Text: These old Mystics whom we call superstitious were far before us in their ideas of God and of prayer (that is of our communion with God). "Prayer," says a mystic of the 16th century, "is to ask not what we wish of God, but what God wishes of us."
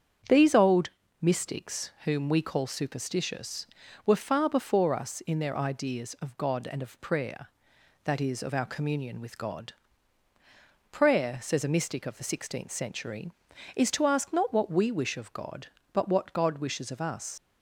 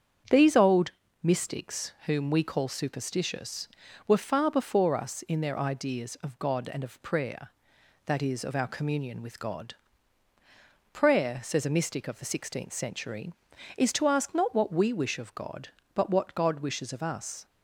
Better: second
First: starts louder than the rest; strong; until 1.6 s; 8 dB // pauses between "old" and "Mystics"; slight; at 0.8 s; 0.32 s long // leaves "us" unfinished; at 17.3 s; 55 ms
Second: starts louder than the rest; strong; until 1.6 s; 8 dB // pauses between "old" and "Mystics"; slight; at 0.9 s; 0.32 s long

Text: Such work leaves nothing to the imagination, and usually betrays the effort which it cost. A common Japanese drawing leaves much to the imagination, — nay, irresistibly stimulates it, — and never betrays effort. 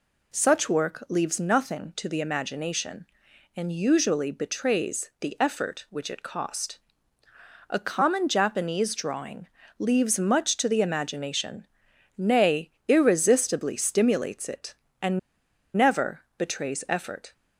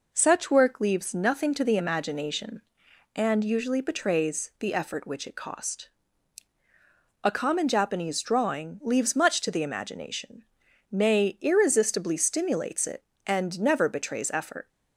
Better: second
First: pauses between "drawing" and "leaves"; slight; at 9.4 s; 0.32 s long // pauses between "and" and "never"; noticeable; at 15.1 s; 0.57 s long // pauses between "never" and "betrays"; slight; at 16.2 s; 0.16 s long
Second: none

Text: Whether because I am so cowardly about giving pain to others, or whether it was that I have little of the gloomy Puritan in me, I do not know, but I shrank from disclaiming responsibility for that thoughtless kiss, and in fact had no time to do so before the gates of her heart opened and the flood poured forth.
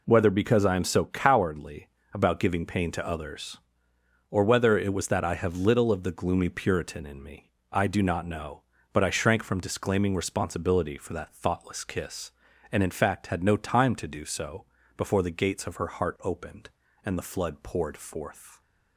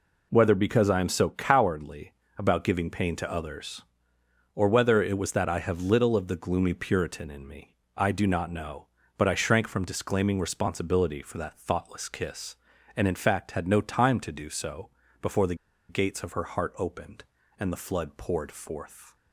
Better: first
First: pauses between "cowardly" and "about"; slight; at 1.8 s; 0.24 s long // pauses between "so" and "before"; slight; at 14.6 s; 0.34 s long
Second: pauses between "cowardly" and "about"; slight; at 2.1 s; 0.24 s long // pauses between "so" and "before"; slight; at 14.8 s; 0.34 s long // pauses between "the" and "gates"; slight; at 15.5 s; 0.34 s long

